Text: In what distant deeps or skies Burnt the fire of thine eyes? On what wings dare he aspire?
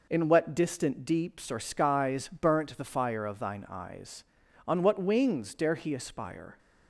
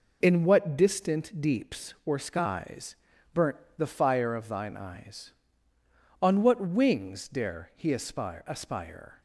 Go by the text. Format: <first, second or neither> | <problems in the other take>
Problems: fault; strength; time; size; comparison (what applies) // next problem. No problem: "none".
first | pauses between "skies" and "Burnt"; at 2.9 s; 0.38 s long // pauses between "Burnt" and "the"; slight; at 3.5 s; 0.20 s long // says "aspire" twice; at 8.4 s